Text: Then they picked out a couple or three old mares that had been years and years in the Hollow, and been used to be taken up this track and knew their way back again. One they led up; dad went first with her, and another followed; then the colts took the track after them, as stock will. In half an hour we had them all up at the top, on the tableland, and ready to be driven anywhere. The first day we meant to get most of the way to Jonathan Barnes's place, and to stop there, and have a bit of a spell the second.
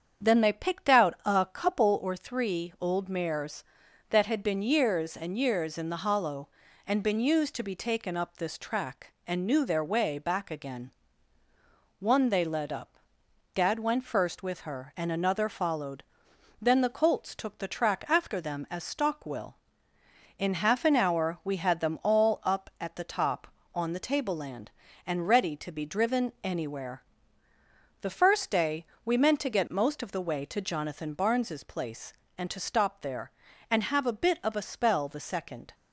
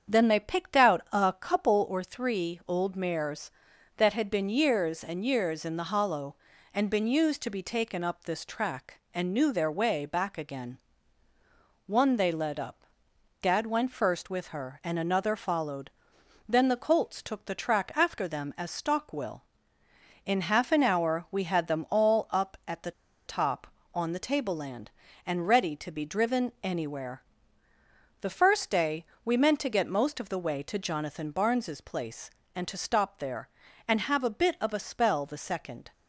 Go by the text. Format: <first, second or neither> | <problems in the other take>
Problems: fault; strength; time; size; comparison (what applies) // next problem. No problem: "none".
first | starts louder than the rest; strong; until 1.1 s; 7.5 dB; strong in the first // pauses between "the" and "top"; slight; at 22.9 s; 0.35 s long // pauses between "day" and "we"; slight; at 29.0 s; 0.22 s long; slight in the first